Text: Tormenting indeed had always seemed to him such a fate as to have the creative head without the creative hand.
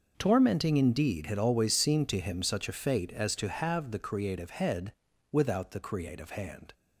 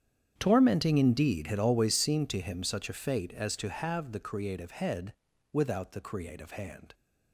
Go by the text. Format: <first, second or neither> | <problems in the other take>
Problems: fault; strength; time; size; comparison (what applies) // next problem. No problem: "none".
first | starts louder than the rest; strong; until 2.1 s; 8.5 dB // pauses between "head" and "without"; at 5.1 s; 0.38 s long; also in the first